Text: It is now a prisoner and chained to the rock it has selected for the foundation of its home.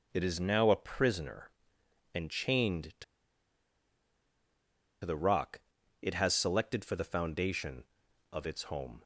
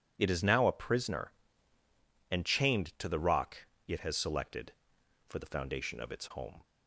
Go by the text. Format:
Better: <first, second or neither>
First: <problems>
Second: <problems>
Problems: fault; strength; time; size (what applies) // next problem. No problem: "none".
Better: second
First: pauses between "to" and "the"; strong; at 3.0 s; 2.0 s long // pauses between "rock" and "it"; at 5.5 s; 0.42 s long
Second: pauses between "rock" and "it"; slight; at 3.6 s; 0.18 s long